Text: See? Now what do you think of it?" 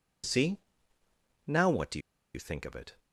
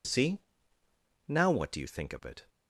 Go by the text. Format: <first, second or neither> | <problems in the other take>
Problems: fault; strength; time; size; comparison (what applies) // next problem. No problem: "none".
second | pauses between "do" and "you"; slight; at 1.9 s; 0.35 s long